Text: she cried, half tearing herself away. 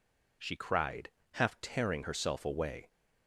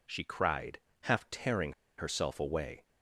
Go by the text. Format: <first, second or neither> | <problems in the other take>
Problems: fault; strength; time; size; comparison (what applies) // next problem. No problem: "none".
first | pauses between "tearing" and "herself"; slight; at 1.7 s; 0.25 s long